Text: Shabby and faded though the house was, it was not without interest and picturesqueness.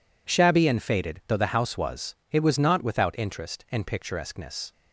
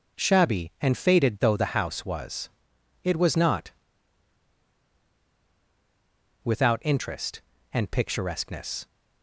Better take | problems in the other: first | pauses between "not" and "without"; strong; at 3.7 s; 2.7 s long

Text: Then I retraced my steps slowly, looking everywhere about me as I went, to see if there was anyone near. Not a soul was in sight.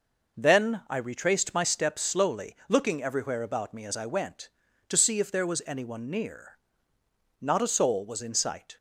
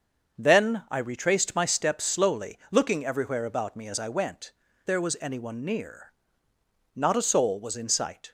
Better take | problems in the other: first | starts louder than the rest; until 1.4 s; 6.5 dB // skips "to see if"; at 4.6 s

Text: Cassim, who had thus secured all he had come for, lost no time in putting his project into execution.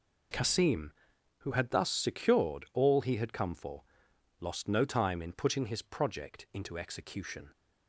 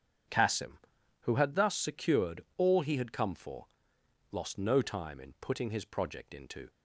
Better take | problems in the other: first | starts louder than the rest; strong; until 1.7 s; 8 dB // stops before "execution"; at 6.6 s

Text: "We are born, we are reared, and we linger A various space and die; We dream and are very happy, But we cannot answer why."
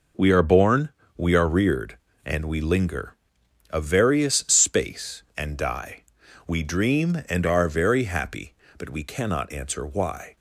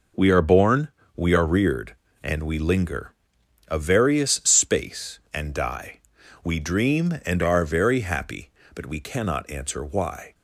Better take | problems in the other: neither | pauses between "linger" and "A"; noticeable; the same in both

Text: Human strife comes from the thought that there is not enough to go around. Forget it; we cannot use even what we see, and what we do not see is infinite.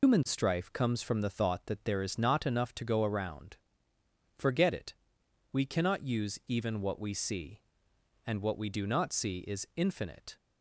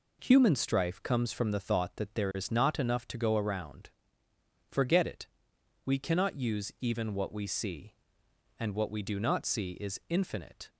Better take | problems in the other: second | loses the start of "Human"; at 0.0 s; 140 ms

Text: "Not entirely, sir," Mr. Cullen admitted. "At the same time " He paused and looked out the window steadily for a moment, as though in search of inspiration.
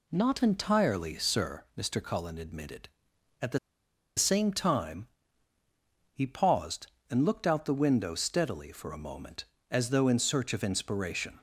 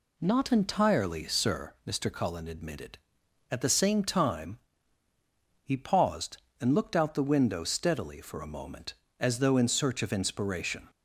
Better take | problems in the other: second | pauses between "the" and "same"; noticeable; at 3.5 s; 0.59 s long

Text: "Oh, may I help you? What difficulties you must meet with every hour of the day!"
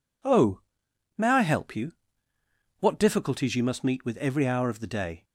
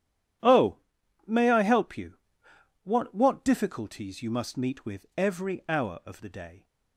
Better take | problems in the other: first | says "What" twice; at 3.1 s

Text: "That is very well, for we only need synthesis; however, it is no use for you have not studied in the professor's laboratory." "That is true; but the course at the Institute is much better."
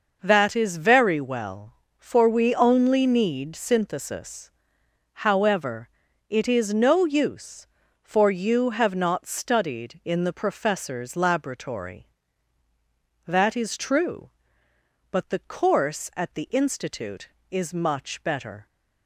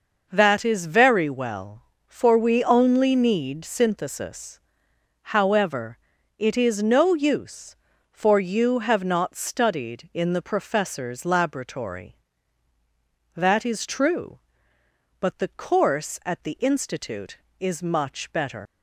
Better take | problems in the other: first | leaves "better" unfinished; at 18.6 s; 110 ms

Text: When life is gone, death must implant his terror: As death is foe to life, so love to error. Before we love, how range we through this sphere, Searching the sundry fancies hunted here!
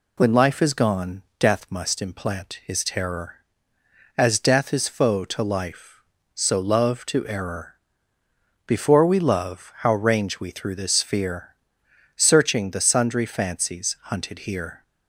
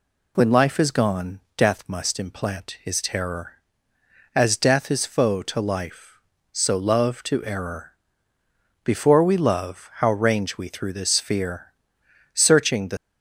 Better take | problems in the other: first | stops before "sundry fancies hunted here"; at 12.9 s

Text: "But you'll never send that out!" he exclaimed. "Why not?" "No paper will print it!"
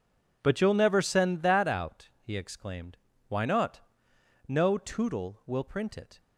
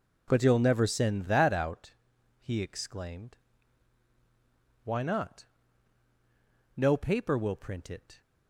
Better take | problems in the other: second | says "tootle" for "paper"; at 4.7 s

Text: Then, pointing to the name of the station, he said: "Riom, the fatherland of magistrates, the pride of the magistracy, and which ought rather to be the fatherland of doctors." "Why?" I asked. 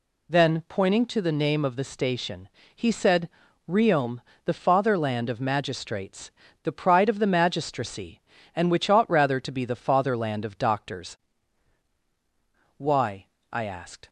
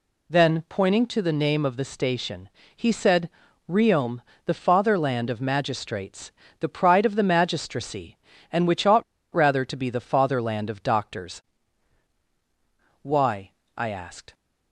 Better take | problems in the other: first | pauses between "ought" and "rather"; slight; at 9.0 s; 0.29 s long

